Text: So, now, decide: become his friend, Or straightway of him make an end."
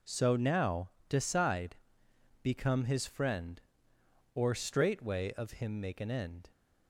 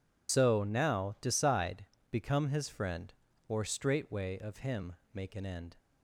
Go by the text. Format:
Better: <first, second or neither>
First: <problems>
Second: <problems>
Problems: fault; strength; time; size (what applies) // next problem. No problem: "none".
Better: first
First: none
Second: loses the start of "So"; at 0.2 s; 60 ms // pauses between "him" and "make"; slight; at 4.9 s; 0.18 s long